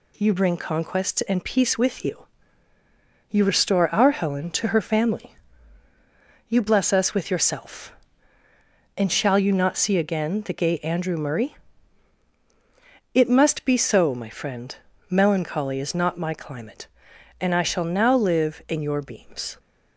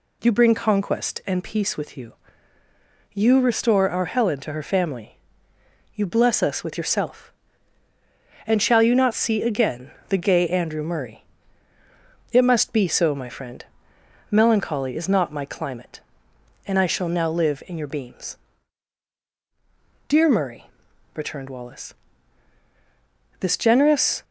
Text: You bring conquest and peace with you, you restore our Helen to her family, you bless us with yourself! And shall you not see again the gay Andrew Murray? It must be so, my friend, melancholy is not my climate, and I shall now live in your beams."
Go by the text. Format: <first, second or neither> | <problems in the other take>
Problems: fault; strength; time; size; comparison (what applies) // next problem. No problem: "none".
first | pauses between "again" and "the"; slight; at 9.9 s; 0.18 s long // goes on to say "Dear Murray returned Wallace this generous"; strong; from 20.0 s on; 4.1 s long